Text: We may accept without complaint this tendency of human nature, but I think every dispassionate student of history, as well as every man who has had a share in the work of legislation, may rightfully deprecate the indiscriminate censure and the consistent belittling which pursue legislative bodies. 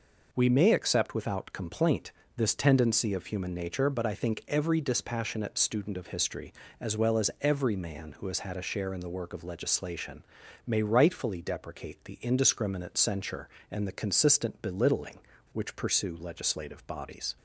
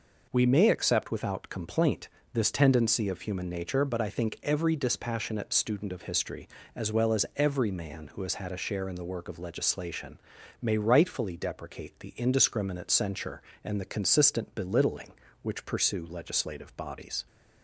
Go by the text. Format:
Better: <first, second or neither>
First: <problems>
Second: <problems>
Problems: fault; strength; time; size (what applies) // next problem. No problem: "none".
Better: neither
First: pauses between "complaint" and "this"; slight; at 2.1 s; 0.24 s long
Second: pauses between "complaint" and "this"; slight; at 2.0 s; 0.24 s long